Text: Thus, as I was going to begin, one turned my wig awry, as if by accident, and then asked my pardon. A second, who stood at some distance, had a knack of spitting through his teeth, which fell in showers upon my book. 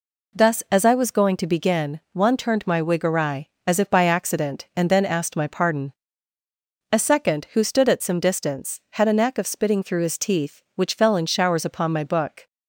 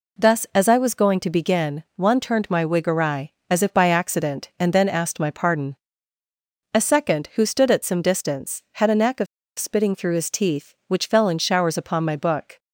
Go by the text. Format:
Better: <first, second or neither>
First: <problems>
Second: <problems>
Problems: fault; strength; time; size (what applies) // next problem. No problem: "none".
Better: first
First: none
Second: pauses between "of" and "spitting"; slight; at 9.2 s; 0.32 s long